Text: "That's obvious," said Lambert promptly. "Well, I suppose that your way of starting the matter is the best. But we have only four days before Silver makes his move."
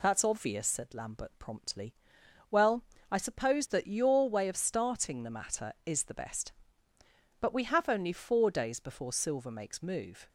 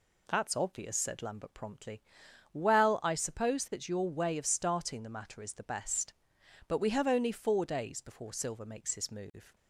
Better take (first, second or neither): second